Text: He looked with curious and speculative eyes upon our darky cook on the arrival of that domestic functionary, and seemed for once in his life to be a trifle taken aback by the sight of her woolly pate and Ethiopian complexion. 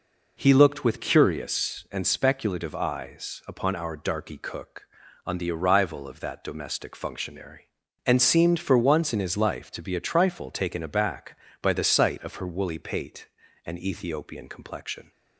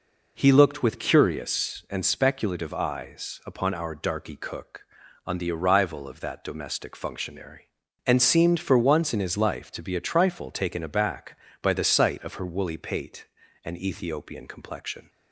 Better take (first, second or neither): neither